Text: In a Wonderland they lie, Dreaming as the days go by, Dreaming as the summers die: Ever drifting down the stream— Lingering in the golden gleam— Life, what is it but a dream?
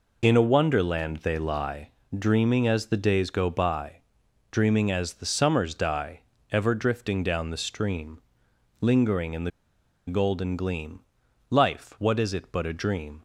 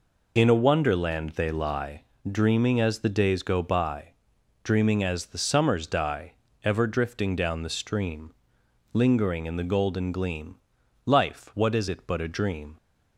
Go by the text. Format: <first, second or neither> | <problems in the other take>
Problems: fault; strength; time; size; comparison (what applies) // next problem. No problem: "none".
second | pauses between "the" and "golden"; noticeable; at 9.5 s; 0.58 s long